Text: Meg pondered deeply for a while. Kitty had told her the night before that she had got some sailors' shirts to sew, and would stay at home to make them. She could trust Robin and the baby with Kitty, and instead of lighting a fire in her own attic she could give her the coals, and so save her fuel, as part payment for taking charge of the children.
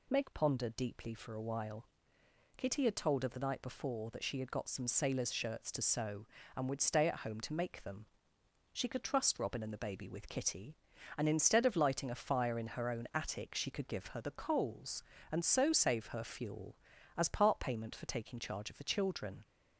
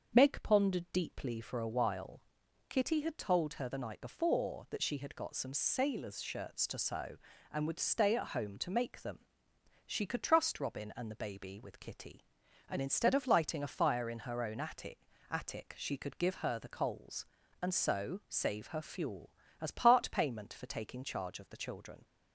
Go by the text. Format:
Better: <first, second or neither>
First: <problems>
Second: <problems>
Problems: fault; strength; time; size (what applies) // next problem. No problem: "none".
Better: first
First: none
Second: starts louder than the rest; until 1.2 s; 6.5 dB // says "attic" twice; at 15.3 s